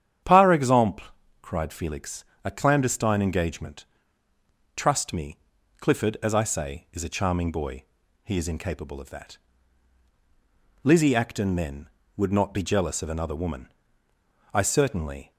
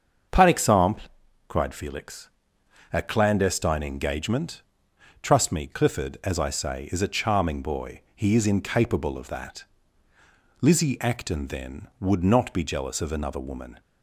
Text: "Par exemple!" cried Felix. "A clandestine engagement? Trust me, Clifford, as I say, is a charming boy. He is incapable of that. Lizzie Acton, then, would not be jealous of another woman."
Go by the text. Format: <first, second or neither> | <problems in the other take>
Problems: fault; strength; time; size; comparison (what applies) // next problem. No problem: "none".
second | starts louder than the rest; strong; until 1.6 s; 9 dB; also in the second // goes on to say "I certainly"; noticeable; from 14.5 s on; 0.78 s long